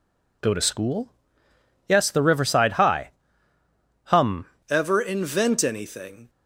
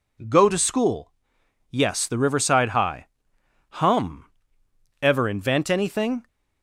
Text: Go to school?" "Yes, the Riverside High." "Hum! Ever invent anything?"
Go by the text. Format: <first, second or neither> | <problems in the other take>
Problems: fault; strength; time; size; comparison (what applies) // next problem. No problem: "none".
second | changes voice at "Ever"; from 4.6 s on; 1.6 s long